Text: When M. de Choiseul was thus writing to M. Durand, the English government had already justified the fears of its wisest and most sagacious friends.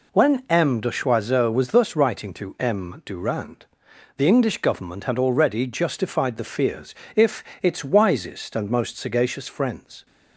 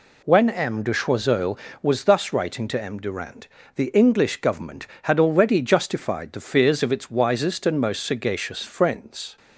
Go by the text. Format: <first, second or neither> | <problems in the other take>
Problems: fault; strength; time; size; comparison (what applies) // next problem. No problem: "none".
second | says "if" for "of"; at 7.1 s